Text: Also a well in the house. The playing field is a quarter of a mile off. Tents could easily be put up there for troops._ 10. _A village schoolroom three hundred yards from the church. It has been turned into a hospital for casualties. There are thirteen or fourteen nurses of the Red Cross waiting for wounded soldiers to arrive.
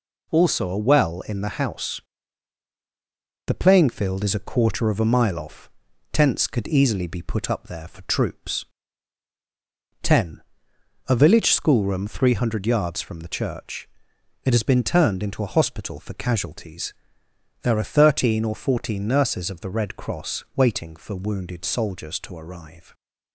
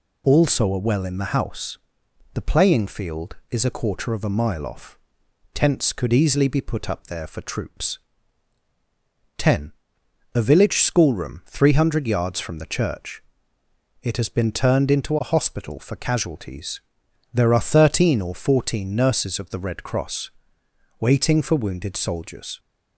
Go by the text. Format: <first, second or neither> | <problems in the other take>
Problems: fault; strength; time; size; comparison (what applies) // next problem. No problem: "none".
first | pauses between "Cross" and "waiting"; noticeable; at 20.3 s; 0.68 s long // stops before "to arrive"; at 22.5 s